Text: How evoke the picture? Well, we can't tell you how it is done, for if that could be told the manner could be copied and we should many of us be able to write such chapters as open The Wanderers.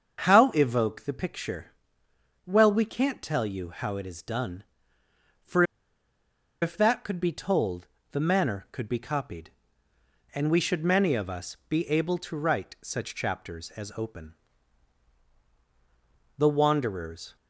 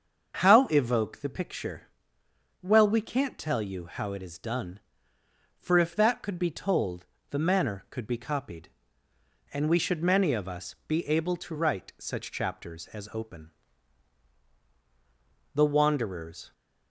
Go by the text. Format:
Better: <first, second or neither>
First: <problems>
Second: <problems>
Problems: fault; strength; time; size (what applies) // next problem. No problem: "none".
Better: second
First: starts louder than the rest; until 1.2 s; 7 dB // pauses between "for" and "if"; at 5.6 s; 0.98 s long // pauses between "told" and "the"; slight; at 7.8 s; 0.24 s long // pauses between "open" and "The"; strong; at 14.3 s; 2.0 s long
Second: starts louder than the rest; until 1.4 s; 6.5 dB // pauses between "told" and "the"; slight; at 7.0 s; 0.24 s long // pauses between "open" and "The"; strong; at 13.5 s; 2.0 s long